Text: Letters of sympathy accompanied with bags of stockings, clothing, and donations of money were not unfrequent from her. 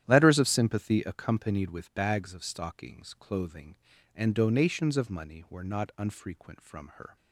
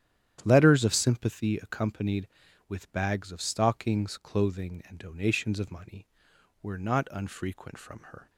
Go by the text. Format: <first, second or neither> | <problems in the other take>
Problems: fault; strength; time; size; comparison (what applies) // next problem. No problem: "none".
neither | starts louder than the rest; strong; the same in both